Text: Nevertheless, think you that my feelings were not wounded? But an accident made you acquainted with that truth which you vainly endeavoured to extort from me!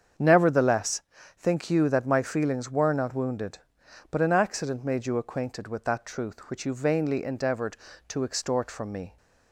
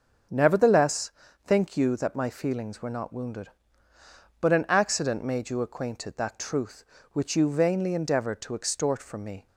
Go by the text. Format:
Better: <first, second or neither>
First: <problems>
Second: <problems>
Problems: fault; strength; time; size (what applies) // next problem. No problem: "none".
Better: first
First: starts louder than the rest; strong; until 1.5 s; 7.5 dB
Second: starts louder than the rest; until 1.6 s; 6.5 dB // skips "with"; at 6.1 s